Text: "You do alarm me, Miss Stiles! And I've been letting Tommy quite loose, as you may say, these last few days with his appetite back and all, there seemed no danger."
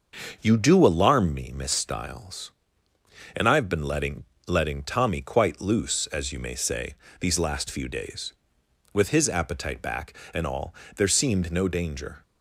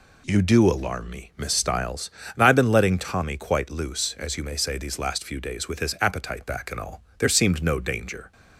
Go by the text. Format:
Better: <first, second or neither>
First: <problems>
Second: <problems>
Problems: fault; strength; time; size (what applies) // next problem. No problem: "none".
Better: second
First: starts louder than the rest; until 1.4 s; 6 dB // says "letting" twice; at 4.4 s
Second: none